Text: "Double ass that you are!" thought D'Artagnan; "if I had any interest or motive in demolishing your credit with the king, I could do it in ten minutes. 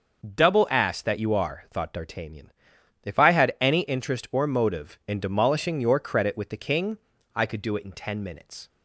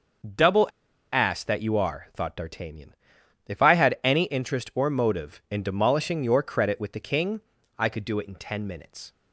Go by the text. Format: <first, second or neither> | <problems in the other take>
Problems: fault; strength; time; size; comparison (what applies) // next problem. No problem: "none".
first | starts louder than the rest; noticeable; until 1.8 s; 6 dB; noticeable in the first // pauses between "Double" and "ass"; at 0.6 s; 0.44 s long